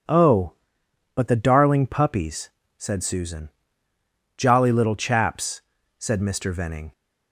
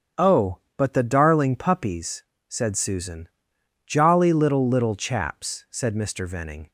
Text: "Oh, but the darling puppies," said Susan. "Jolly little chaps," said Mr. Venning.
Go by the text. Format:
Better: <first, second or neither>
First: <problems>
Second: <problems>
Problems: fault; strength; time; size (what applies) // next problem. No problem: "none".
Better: first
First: none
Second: starts louder than the rest; strong; until 1.3 s; 8 dB // says "little" twice; at 4.6 s